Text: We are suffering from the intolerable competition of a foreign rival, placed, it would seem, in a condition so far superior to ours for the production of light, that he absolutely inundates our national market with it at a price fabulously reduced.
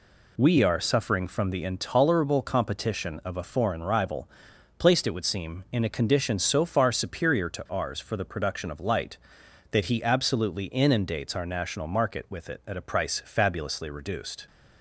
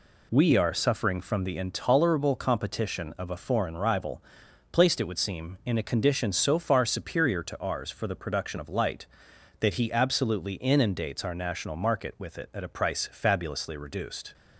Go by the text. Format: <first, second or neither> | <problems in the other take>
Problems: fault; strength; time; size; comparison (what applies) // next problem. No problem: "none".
neither | none